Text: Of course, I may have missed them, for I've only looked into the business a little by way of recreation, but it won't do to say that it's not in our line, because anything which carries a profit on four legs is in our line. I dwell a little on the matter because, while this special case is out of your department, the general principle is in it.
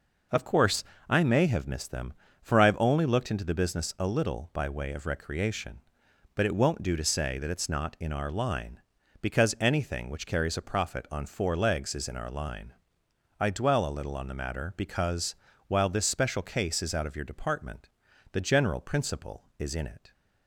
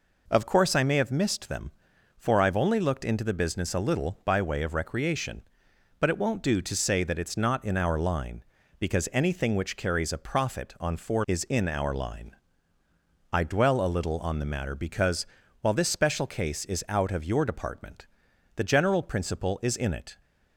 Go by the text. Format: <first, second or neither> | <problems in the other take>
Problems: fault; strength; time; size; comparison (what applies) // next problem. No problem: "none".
first | skips "legs"; at 11.2 s